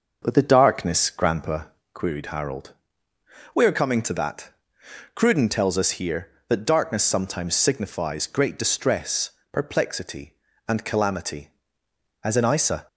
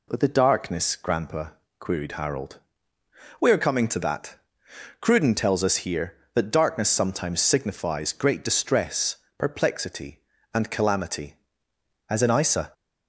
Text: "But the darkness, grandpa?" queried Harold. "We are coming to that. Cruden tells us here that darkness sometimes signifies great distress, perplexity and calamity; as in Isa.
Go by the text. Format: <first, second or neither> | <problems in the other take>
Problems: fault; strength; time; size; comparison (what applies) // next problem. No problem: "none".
second | starts louder than the rest; noticeable; until 2.0 s; 6 dB